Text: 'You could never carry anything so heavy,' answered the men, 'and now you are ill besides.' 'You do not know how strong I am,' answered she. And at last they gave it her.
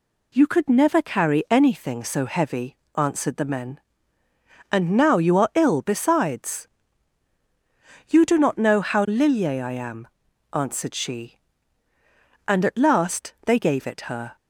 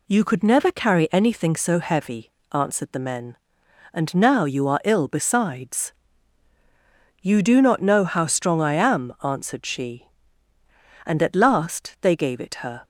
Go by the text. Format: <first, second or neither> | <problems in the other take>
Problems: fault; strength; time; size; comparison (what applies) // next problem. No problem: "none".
second | says "lilye" for "strong"; at 9.0 s